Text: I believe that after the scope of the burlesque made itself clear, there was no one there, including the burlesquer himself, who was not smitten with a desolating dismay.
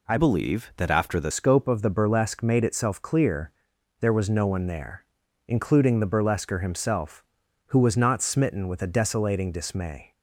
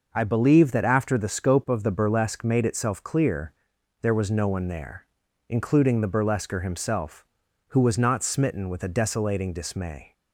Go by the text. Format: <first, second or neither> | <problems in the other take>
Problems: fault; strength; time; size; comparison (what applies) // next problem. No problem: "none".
second | changes voice from "believe" to "the"; from 0.1 to 1.3 s; 1.2 s long